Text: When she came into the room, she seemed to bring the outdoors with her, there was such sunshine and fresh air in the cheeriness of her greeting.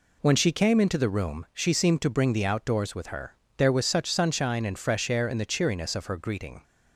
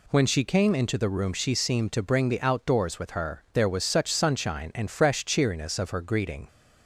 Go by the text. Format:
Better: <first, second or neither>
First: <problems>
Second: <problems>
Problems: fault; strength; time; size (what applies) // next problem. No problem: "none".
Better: first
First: none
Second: skips "air in the"; at 5.2 s